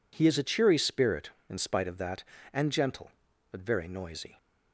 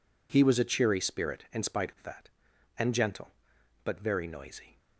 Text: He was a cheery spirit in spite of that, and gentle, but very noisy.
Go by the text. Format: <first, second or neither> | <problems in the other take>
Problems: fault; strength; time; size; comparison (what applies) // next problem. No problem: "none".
second | says "is" for "was"; at 0.3 s